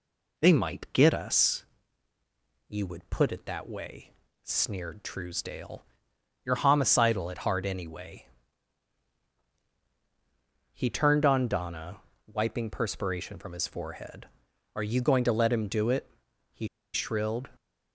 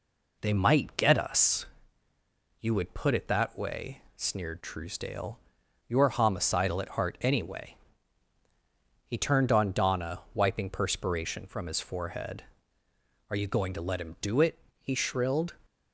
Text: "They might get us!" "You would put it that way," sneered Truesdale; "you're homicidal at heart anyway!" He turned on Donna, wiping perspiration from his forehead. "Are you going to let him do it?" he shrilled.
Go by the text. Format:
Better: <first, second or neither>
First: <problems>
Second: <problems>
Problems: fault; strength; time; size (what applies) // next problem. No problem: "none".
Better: second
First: pauses between "he" and "shrilled"; slight; at 16.6 s; 0.26 s long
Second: none